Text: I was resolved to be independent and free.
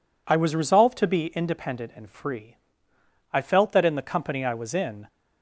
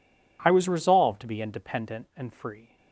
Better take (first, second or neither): second